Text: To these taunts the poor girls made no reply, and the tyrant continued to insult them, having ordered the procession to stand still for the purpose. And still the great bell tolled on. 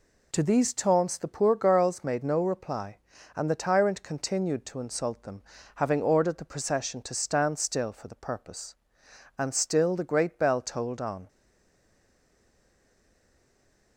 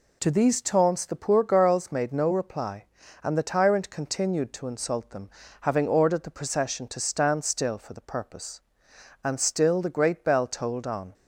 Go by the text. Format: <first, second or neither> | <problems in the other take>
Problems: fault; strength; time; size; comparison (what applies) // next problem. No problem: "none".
second | stays silent after the last word; strong; from 11.2 s on; 2.7 s long